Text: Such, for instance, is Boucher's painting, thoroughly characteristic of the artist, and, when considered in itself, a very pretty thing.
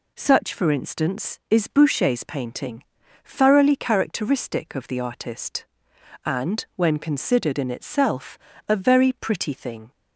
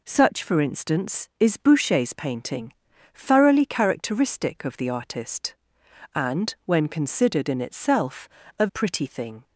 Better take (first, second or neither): first